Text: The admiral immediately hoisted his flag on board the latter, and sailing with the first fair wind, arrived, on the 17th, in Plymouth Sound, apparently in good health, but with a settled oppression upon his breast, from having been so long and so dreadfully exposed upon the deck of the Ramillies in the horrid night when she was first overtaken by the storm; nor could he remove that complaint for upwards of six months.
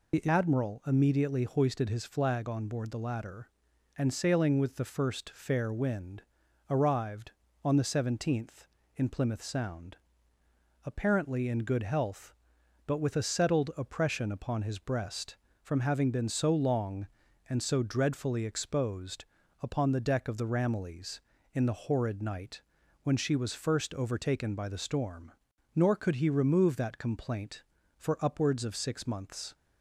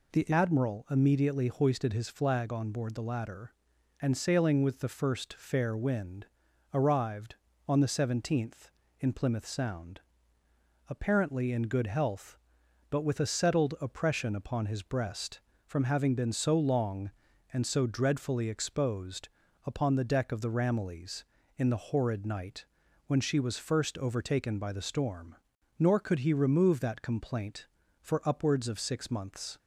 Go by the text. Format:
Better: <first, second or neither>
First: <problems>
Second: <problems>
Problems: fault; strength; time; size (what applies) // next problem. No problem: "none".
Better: second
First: loses the start of "The"; at 0.1 s; 50 ms // pauses between "exposed" and "upon"; at 19.2 s; 0.38 s long // pauses between "night" and "when"; at 22.6 s; 0.42 s long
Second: pauses between "exposed" and "upon"; at 19.2 s; 0.38 s long // pauses between "night" and "when"; at 22.6 s; 0.42 s long